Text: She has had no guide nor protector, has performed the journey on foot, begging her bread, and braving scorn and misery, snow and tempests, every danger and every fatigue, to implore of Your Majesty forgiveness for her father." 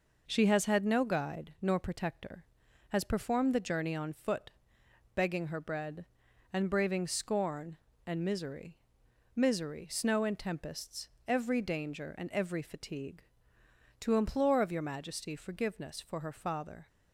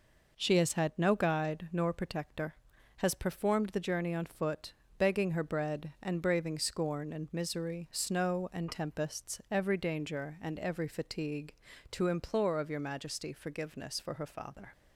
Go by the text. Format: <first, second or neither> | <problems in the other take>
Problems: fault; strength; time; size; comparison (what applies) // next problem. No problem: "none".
second | says "misery" twice; at 9.3 s